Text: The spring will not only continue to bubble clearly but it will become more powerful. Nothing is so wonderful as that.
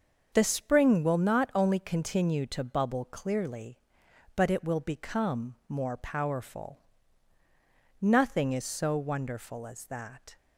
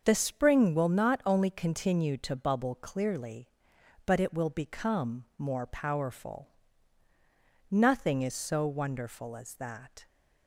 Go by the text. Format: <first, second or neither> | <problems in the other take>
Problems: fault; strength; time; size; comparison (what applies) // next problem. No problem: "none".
neither | starts louder than the rest; the same in both